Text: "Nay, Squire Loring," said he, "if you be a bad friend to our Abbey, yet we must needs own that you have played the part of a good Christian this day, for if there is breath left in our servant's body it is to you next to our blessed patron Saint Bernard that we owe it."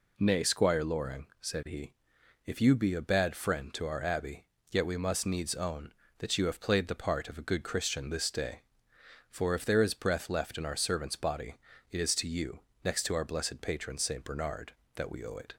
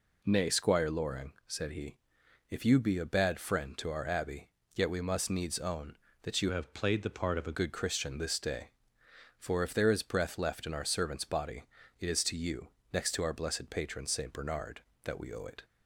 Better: first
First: pauses between "body" and "it"; slight; at 11.5 s; 0.34 s long // pauses between "you" and "next"; slight; at 12.5 s; 0.24 s long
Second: changes voice from "have" to "a"; from 6.5 to 7.5 s; 1.0 s long // pauses between "body" and "it"; slight; at 11.6 s; 0.34 s long // pauses between "you" and "next"; slight; at 12.6 s; 0.24 s long

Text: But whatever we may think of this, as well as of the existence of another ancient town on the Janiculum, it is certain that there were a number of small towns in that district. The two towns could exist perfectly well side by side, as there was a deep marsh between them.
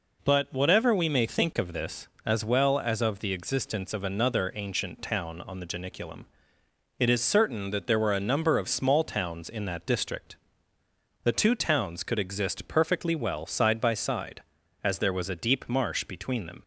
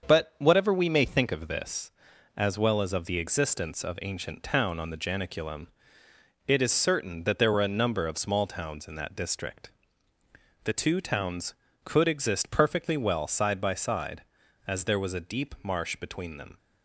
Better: first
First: none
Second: starts louder than the rest; until 1.1 s; 6.5 dB // skips "another"; at 3.9 s

